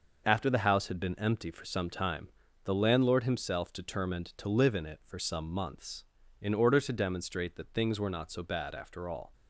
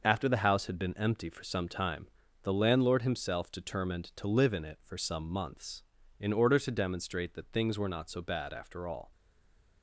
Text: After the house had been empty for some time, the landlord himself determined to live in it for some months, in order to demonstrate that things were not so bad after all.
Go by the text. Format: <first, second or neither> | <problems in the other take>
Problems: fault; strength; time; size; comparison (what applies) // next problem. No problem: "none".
first | stays silent after the last word; slight; from 9.1 s on; 0.7 s long